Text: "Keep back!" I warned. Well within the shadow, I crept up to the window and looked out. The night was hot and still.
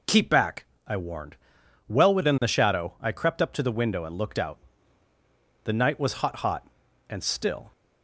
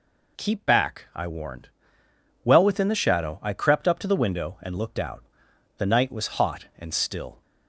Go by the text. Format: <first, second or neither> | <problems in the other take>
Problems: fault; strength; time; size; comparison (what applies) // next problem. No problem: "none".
second | says "hot" twice; at 6.3 s